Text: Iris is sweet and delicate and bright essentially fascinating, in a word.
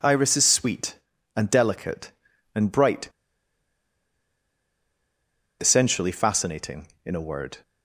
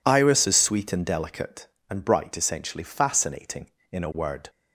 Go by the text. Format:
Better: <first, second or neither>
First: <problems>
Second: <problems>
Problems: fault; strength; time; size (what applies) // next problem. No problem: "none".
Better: second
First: pauses between "bright" and "essentially"; strong; at 3.0 s; 2.5 s long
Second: none